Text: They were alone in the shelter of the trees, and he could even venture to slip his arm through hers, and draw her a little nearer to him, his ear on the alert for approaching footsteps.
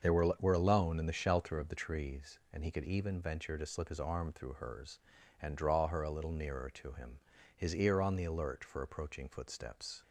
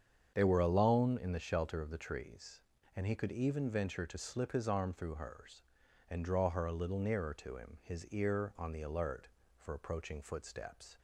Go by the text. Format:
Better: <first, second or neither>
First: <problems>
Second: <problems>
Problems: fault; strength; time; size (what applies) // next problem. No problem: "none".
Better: second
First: starts louder than the rest; until 1.0 s; 6.5 dB // says "were" twice; at 0.4 s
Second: starts louder than the rest; strong; until 1.3 s; 7.5 dB